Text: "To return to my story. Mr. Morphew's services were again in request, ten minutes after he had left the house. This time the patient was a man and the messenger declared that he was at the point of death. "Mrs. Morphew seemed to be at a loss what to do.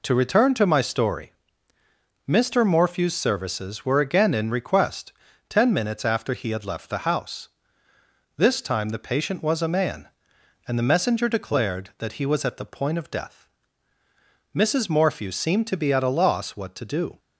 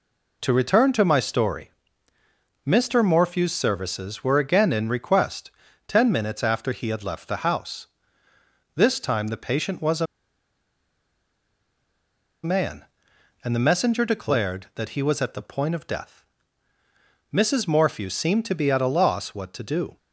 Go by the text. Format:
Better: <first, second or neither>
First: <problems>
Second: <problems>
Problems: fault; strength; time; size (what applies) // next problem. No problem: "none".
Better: first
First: none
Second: pauses between "a" and "man"; strong; at 10.0 s; 2.3 s long